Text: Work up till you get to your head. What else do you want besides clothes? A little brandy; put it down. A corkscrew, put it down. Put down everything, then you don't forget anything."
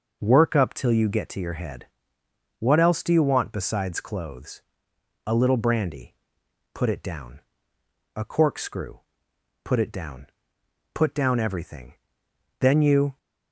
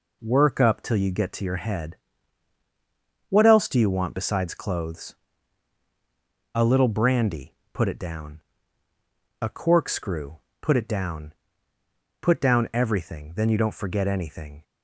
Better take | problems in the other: second | stops before "don't forget anything"; at 13.1 s

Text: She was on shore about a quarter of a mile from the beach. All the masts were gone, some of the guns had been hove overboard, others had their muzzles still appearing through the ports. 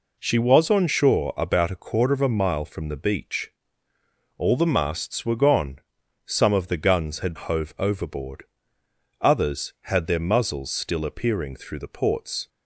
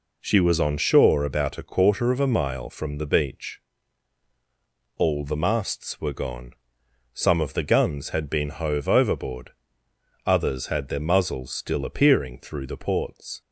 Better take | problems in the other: second | skips "been"; at 7.3 s

